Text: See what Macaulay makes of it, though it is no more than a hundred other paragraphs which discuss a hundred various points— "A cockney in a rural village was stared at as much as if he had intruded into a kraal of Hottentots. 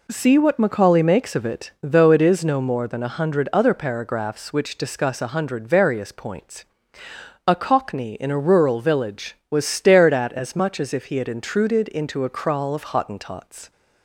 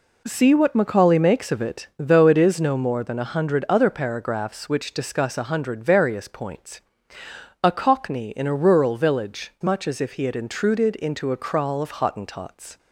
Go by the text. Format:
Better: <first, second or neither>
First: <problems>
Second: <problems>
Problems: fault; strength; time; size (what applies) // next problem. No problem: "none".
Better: first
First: none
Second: skips "was stared at as"; at 9.5 s